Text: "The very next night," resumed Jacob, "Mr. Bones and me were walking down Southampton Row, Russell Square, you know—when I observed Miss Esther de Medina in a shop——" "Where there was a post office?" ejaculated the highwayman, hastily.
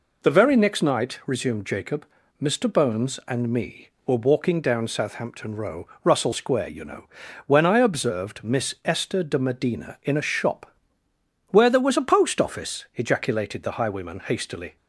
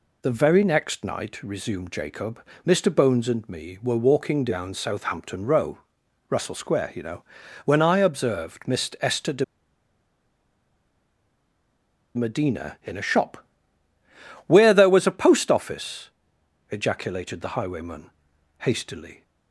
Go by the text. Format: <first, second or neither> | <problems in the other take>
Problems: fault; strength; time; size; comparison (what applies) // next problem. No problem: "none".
first | pauses between "de" and "Medina"; strong; at 9.4 s; 2.7 s long